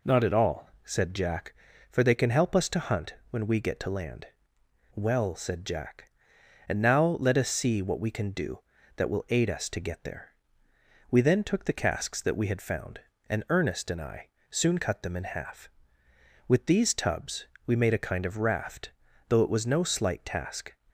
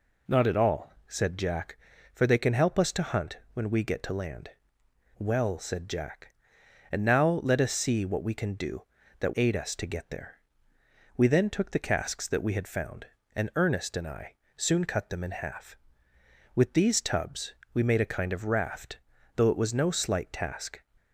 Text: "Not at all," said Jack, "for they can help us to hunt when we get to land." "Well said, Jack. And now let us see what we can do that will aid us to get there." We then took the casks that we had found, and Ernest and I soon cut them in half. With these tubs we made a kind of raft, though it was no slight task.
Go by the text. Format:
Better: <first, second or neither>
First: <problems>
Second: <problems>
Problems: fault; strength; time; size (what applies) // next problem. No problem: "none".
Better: first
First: pauses between "hunt" and "when"; slight; at 3.1 s; 0.16 s long // pauses between "I" and "soon"; slight; at 14.2 s; 0.22 s long // pauses between "tubs" and "we"; slight; at 17.4 s; 0.20 s long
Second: pauses between "hunt" and "when"; slight; at 3.3 s; 0.16 s long // skips "will"; at 9.3 s // pauses between "I" and "soon"; slight; at 14.3 s; 0.22 s long // pauses between "tubs" and "we"; slight; at 17.5 s; 0.20 s long